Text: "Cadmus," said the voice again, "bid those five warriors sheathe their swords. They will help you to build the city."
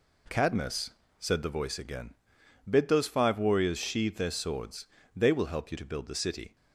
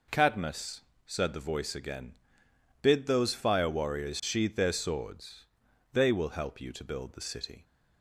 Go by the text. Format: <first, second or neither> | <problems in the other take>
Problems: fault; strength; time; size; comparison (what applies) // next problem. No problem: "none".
first | says "fire" for "five"; at 3.3 s